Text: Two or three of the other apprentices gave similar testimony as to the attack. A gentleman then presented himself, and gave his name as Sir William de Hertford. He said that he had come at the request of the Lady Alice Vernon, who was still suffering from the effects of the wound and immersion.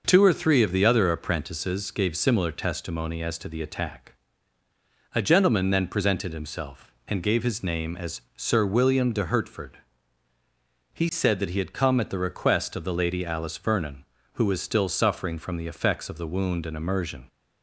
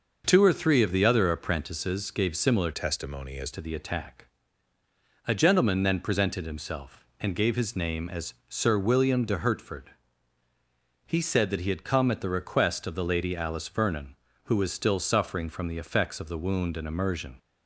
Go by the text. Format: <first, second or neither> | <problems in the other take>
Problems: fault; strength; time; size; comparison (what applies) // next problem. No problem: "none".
first | changes voice from "testimony" to "as"; from 2.7 to 3.5 s; 0.8 s long